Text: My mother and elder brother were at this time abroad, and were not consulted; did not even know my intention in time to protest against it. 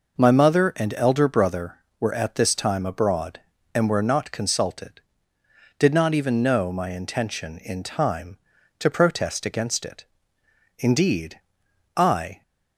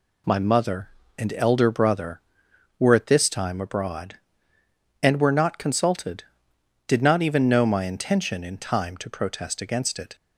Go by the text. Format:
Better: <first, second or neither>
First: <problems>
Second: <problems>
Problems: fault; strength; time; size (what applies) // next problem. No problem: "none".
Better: second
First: goes on to say "Indeed I"; from 10.7 s on; 1.6 s long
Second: none